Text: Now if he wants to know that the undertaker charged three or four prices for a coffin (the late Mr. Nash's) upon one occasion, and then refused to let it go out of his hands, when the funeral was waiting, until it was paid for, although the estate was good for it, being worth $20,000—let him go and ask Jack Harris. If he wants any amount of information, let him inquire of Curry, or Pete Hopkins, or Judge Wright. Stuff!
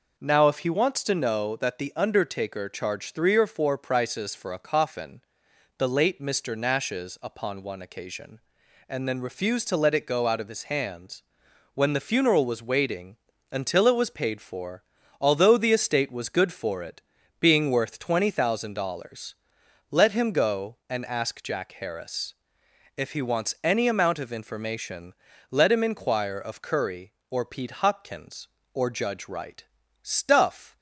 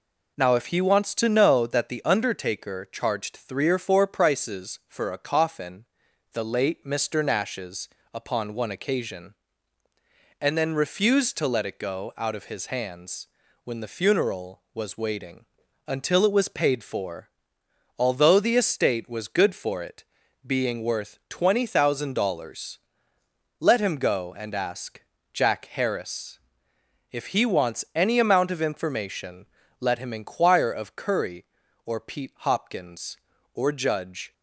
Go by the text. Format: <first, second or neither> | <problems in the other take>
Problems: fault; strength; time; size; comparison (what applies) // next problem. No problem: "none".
first | pauses between "ask" and "Jack"; slight; at 25.0 s; 0.28 s long // stops before "Wright Stuff"; at 34.3 s